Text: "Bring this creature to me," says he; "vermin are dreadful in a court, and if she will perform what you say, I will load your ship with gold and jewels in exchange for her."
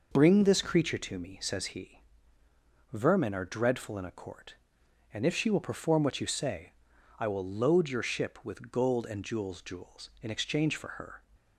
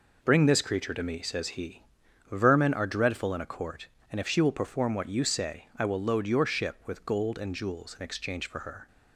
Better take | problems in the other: second | says "jewels" twice; at 9.6 s

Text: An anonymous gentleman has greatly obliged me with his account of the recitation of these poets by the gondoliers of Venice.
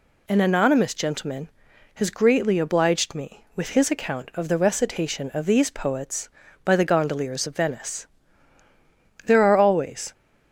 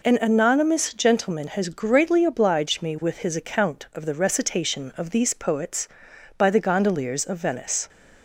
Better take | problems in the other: second | goes on to say "There are always"; noticeable; from 9.2 s on; 0.88 s long

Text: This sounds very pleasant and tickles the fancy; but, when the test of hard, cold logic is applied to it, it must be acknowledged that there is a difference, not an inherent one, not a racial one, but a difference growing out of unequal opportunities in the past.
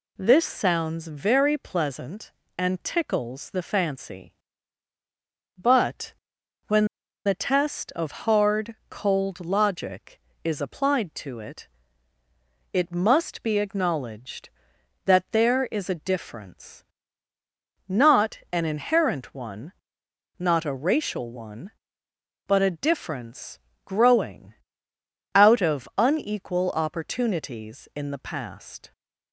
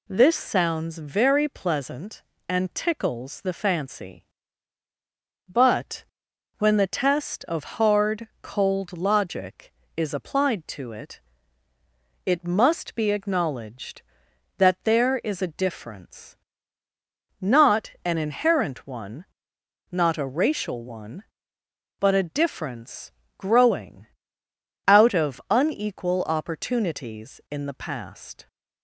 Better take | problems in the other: second | pauses between "when" and "the"; at 6.8 s; 0.39 s long // pauses between "difference" and "growing"; slight; at 23.5 s; 0.28 s long; slight in the second // pauses between "growing" and "out"; noticeable; at 24.5 s; 0.80 s long; noticeable in the second

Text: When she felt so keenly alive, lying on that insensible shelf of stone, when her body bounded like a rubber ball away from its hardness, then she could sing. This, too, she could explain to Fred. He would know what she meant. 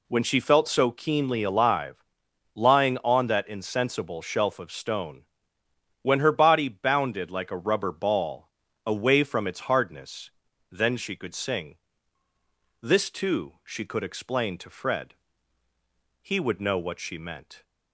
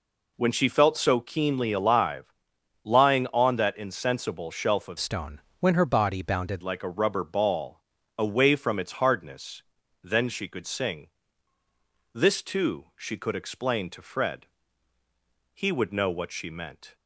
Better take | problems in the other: first | changes voice from "stone" to "bounded"; from 4.9 to 6.6 s; 1.7 s long // pauses between "ball" and "away"; slight; at 7.8 s; 0.36 s long; slight in the first

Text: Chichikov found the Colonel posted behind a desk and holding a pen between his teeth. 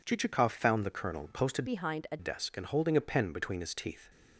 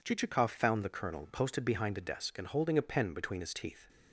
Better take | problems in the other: second | changes voice from "behind" to "a"; from 1.6 to 2.1 s; 0.5 s long

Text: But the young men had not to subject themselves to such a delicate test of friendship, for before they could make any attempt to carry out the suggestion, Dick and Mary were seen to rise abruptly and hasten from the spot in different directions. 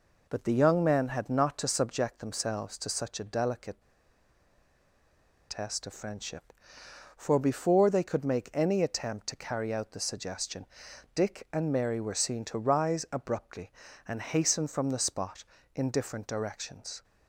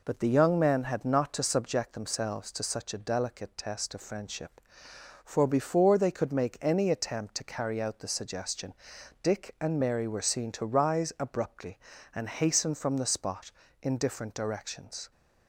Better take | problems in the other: second | pauses between "delicate" and "test"; strong; at 3.8 s; 1.6 s long

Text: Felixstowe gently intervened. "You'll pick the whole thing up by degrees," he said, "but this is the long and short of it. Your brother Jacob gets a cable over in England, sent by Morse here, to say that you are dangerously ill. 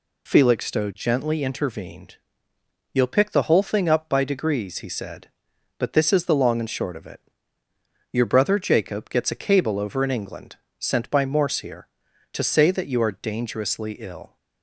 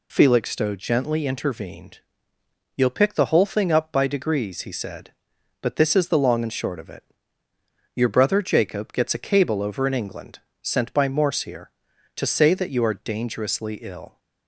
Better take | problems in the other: neither | none

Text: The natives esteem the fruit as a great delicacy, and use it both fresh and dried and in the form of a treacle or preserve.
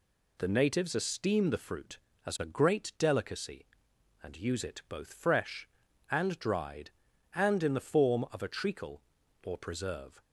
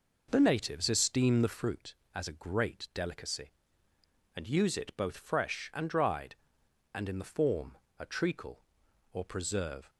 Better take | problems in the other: first | skips "of"; at 7.8 s

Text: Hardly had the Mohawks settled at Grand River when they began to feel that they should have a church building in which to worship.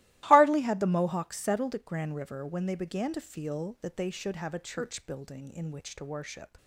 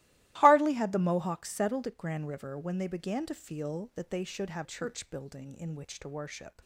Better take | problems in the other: first | starts louder than the rest; strong; until 1.4 s; 17 dB; strong in the first // skips "a"; at 4.6 s

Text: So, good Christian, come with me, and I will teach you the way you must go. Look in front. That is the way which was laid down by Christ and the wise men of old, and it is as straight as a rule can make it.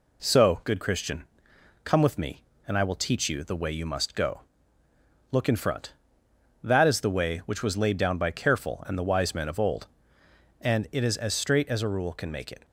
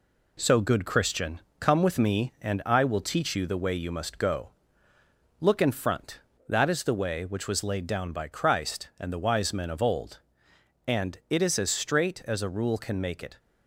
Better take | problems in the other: second | says "Careful" for "Christ"; at 8.2 s

